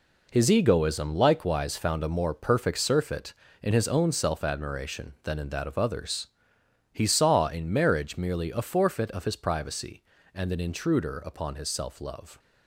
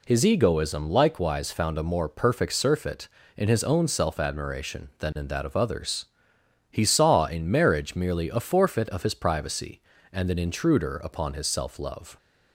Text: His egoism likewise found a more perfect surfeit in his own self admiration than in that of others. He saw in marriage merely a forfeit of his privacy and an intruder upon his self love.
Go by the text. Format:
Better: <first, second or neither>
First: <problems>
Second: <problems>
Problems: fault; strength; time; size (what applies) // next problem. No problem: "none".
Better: second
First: gets quieter; strong; throughout; 9 dB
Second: none